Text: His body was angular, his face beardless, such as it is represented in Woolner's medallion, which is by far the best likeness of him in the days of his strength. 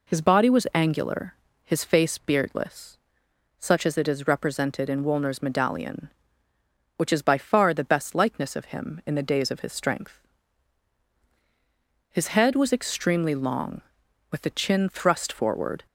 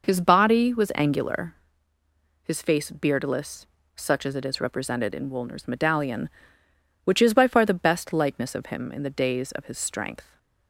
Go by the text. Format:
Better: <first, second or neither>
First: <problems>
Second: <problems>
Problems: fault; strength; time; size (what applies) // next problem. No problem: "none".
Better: second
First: goes on to say "His head was extremely long with the chin thrust forward"; strong; from 12.0 s on; 3.7 s long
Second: none